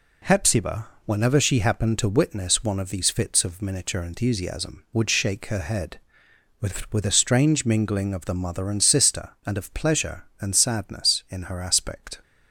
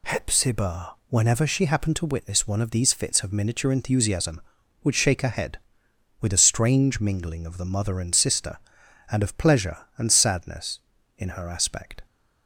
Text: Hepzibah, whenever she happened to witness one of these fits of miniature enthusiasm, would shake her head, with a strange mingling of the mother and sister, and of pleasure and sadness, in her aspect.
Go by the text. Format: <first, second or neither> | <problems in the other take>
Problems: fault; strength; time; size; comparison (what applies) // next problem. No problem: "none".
second | says "with" twice; at 6.9 s